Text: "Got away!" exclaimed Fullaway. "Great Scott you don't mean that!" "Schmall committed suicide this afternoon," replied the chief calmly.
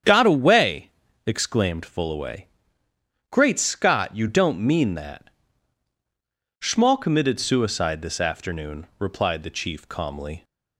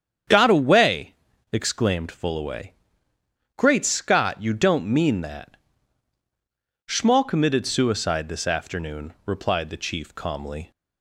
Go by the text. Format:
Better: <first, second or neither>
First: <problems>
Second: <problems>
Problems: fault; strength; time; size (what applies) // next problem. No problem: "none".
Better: neither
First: starts louder than the rest; strong; until 1.3 s; 8 dB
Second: starts louder than the rest; strong; until 1.6 s; 8 dB